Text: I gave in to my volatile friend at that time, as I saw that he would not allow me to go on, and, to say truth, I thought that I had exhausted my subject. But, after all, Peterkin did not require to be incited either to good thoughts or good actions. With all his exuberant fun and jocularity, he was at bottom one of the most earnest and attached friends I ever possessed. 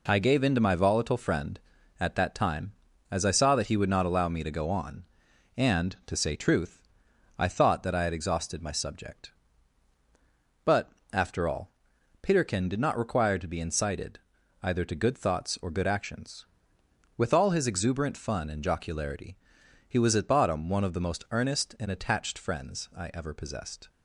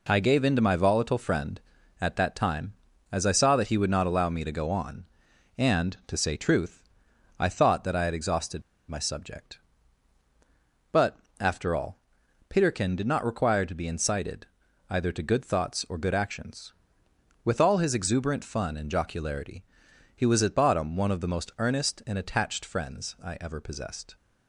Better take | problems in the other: first | pauses between "exhausted" and "my"; slight; at 8.6 s; 0.27 s long // pauses between "incited" and "either"; at 14.4 s; 0.44 s long; also in the first

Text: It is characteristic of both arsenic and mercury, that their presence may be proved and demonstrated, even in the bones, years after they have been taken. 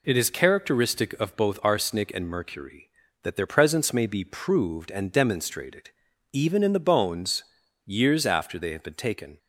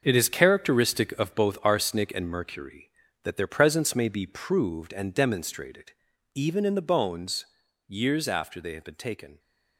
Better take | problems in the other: first | gets quieter; strong; throughout; 9.5 dB

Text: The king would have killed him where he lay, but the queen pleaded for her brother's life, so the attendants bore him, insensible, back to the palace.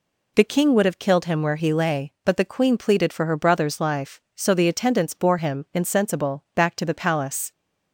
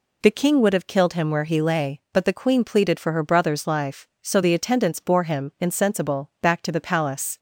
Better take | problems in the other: neither | none

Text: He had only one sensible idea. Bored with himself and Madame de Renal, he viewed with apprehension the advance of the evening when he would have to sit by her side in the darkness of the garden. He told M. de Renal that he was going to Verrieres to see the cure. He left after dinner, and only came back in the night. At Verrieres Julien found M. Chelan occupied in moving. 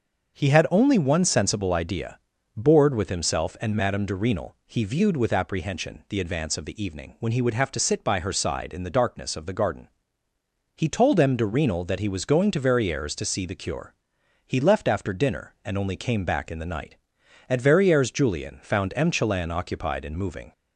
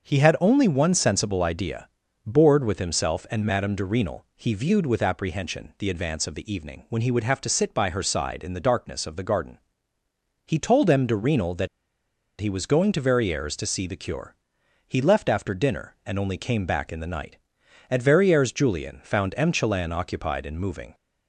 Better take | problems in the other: first | starts louder than the rest; until 1.1 s; 6.5 dB; also in the first // pauses between "that" and "he"; noticeable; at 11.6 s; 0.72 s long

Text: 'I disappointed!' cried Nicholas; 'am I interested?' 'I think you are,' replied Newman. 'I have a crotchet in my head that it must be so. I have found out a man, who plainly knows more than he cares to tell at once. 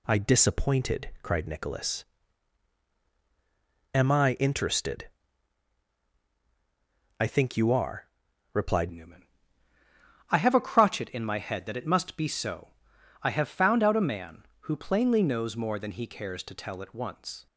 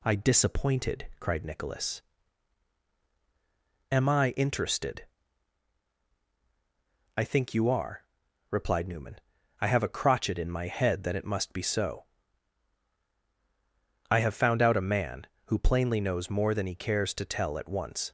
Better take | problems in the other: second | changes voice at "Newman"; from 8.9 s on; 8.5 s long

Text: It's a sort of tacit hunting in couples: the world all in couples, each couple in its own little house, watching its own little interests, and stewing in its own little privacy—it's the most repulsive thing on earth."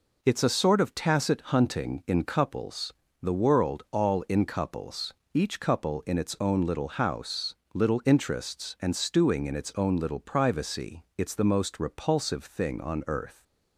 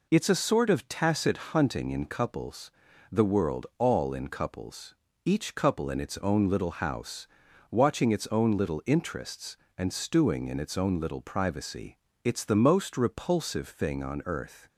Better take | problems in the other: second | skips "watching its own"; at 7.6 s

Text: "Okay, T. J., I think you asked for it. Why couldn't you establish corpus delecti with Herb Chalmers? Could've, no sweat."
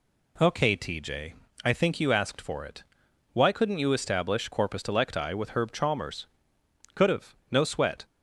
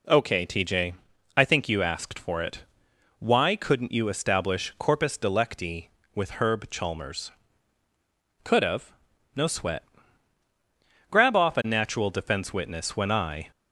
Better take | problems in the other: first | goes on to say "Grab off a natural defense witness when I"; strong; from 11.0 s on; 2.4 s long

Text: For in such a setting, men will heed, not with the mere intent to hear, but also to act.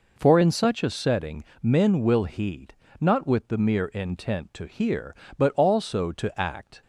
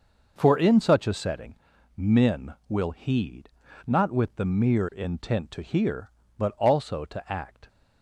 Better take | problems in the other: neither | none

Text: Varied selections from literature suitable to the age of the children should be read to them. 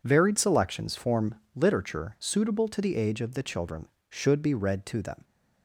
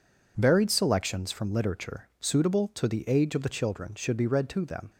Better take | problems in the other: second | says "form" for "from"; at 0.9 s

